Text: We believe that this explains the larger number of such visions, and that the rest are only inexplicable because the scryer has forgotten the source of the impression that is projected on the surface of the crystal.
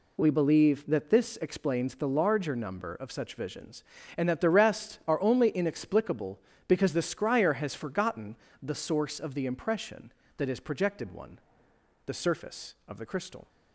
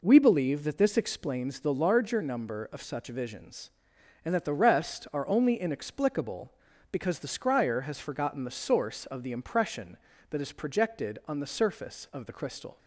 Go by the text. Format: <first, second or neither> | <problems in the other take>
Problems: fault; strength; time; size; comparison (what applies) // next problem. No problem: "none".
second | pauses between "forgotten" and "the"; slight; at 8.3 s; 0.28 s long // says "one" for "on"; at 11.1 s